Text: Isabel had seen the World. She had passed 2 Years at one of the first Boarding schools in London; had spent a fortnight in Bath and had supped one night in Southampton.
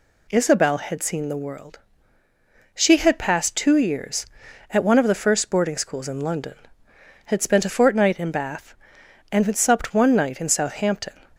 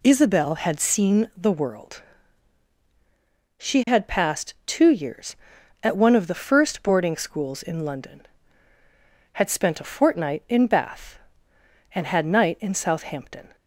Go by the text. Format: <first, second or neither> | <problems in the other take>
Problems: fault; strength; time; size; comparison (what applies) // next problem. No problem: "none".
first | skips "supped one"; at 12.2 s